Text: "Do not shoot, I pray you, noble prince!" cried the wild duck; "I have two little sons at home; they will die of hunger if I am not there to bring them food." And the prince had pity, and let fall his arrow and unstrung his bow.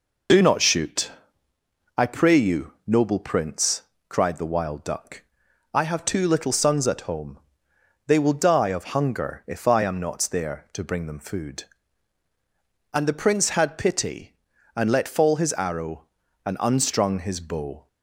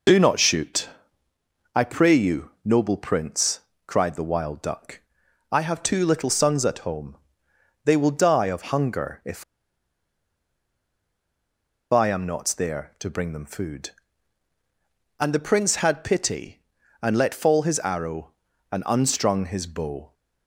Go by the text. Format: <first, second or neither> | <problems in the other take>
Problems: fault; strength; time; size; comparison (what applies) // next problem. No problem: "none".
first | pauses between "if" and "I"; strong; at 9.4 s; 2.4 s long